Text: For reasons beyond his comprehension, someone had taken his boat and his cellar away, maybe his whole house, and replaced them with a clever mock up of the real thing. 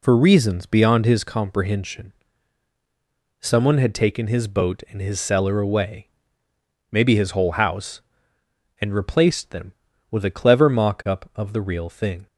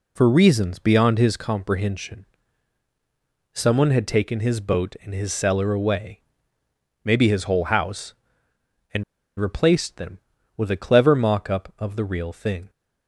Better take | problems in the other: first | pauses between "and" and "replaced"; slight; at 9.0 s; 0.35 s long

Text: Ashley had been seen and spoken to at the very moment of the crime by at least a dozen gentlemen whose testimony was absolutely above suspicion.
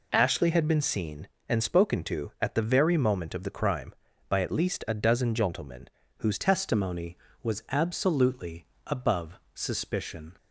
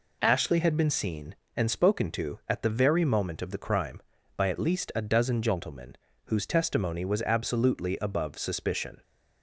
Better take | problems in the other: second | pauses between "gentlemen" and "whose"; slight; at 5.8 s; 0.30 s long; slight in the second // changes voice at "testimony"; from 6.3 s on; 4.0 s long // pauses between "absolutely" and "above"; slight; at 8.6 s; 0.20 s long // pauses between "above" and "suspicion"; slight; at 9.3 s; 0.16 s long

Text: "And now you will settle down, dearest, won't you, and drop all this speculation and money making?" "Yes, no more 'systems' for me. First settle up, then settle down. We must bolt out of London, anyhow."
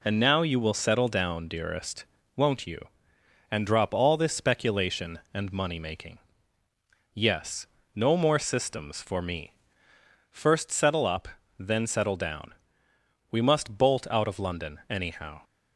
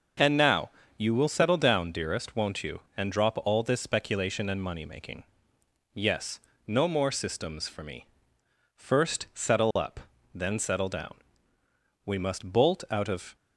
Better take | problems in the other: first | starts louder than the rest; noticeable; until 1.4 s; 6 dB // pauses between "now" and "you"; slight; at 0.7 s; 0.26 s long // stops before "London anyhow"; at 13.3 s

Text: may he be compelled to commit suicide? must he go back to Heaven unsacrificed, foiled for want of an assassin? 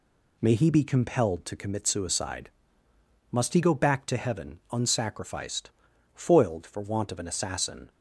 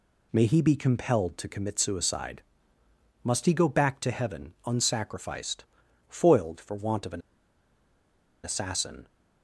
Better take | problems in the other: first | pauses between "an" and "assassin"; at 7.2 s; 1.2 s long

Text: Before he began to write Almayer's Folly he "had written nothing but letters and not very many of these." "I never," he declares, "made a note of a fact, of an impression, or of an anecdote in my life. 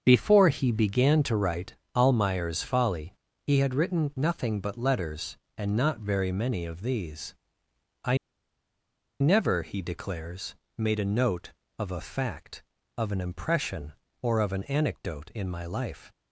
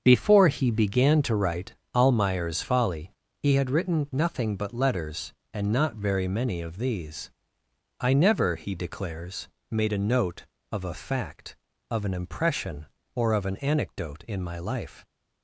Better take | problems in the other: second | starts louder than the rest; until 1.0 s; 7 dB; also in the second // pauses between "write" and "Almayer's"; slight; at 1.7 s; 0.20 s long; slight in the second // pauses between "Folly" and "he"; slight; at 3.1 s; 0.32 s long; slight in the second // pauses between "I" and "never"; at 8.1 s; 1.0 s long

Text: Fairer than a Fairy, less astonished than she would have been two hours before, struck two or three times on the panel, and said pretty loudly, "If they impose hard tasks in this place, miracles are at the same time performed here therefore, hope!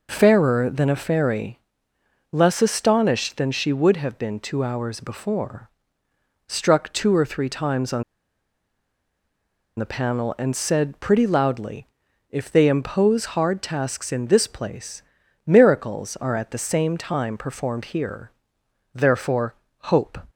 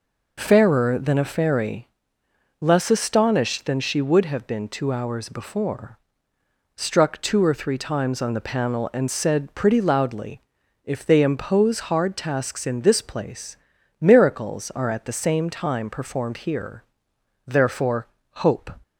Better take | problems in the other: second | pauses between "on" and "the"; strong; at 8.0 s; 1.7 s long // pauses between "here" and "therefore"; noticeable; at 18.3 s; 0.64 s long; noticeable in the second

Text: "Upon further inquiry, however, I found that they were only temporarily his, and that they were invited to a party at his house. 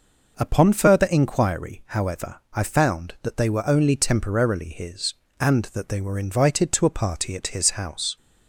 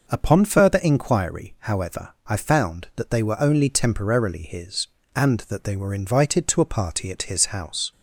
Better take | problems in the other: neither | none

